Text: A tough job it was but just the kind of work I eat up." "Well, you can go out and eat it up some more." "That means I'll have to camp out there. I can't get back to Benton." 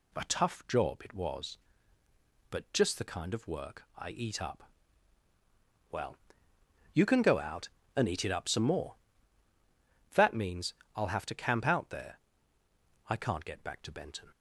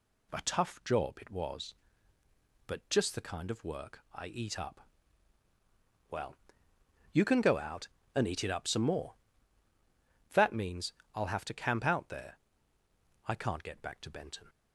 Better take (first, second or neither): neither